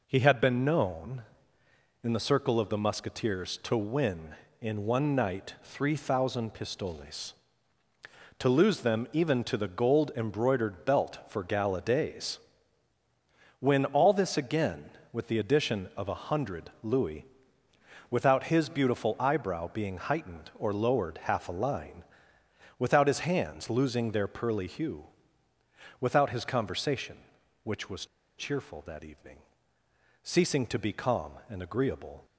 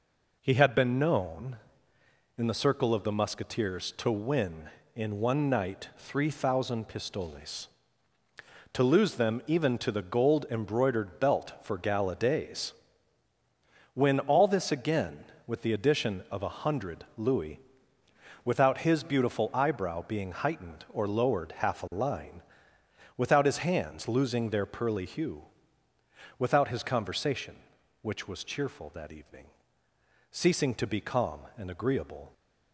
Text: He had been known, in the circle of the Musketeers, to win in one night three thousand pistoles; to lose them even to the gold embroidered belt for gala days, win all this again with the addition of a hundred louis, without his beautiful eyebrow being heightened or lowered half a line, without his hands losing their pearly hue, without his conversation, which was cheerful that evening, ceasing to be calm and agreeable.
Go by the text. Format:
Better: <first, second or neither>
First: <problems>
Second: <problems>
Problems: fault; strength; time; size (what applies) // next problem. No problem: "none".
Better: second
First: pauses between "was" and "cheerful"; slight; at 28.0 s; 0.33 s long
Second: none